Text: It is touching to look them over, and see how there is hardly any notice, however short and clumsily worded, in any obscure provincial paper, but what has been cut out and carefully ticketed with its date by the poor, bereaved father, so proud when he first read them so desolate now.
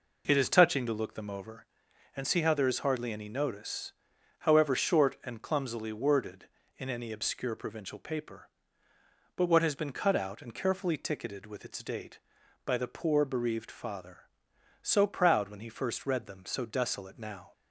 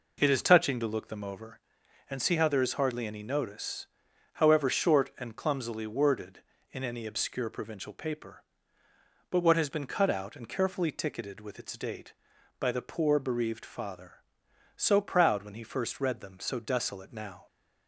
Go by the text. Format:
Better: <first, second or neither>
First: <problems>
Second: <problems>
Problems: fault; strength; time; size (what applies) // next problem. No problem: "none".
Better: neither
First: none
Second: none